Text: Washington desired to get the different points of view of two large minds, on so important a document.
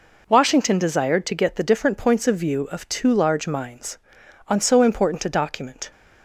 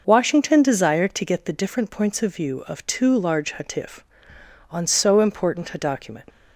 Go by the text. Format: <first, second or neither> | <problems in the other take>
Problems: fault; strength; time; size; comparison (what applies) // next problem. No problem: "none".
first | says "hatif" for "minds"; at 3.5 s